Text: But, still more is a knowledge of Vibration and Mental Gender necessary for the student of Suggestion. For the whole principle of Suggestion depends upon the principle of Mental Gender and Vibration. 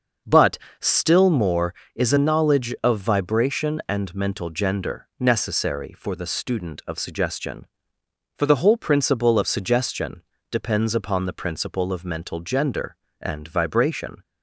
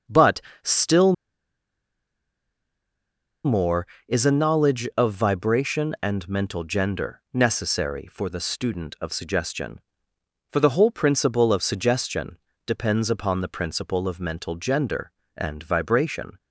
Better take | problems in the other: first | starts louder than the rest; until 3.6 s; 6.5 dB; also in the first // pauses between "still" and "more"; strong; at 1.1 s; 2.3 s long // pauses between "Suggestion" and "depends"; slight; at 12.3 s; 0.28 s long; slight in the first

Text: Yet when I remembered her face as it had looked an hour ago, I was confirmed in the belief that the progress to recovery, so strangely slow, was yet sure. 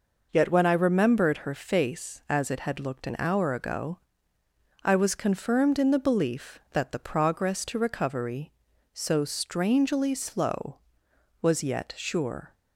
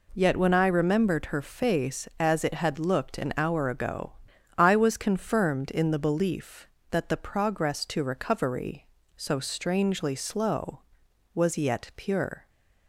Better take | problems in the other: first | says "pure" for "sure"; at 11.9 s

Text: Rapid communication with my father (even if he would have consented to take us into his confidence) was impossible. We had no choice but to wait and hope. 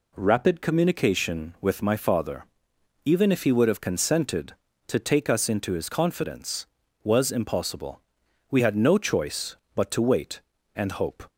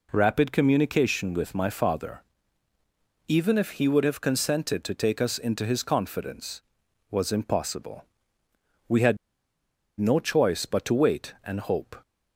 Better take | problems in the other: first | pauses between "had" and "no"; noticeable; at 9.1 s; 0.83 s long

